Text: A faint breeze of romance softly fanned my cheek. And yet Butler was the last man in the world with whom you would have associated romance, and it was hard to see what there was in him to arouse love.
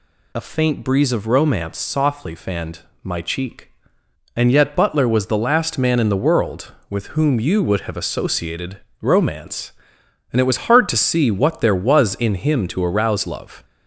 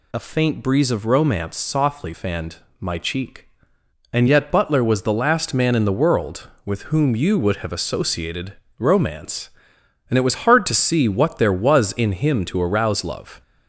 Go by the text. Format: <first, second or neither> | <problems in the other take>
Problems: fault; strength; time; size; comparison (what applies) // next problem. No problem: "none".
neither | pauses between "fanned" and "my"; slight; the same in both // pauses between "associated" and "romance"; slight; the same in both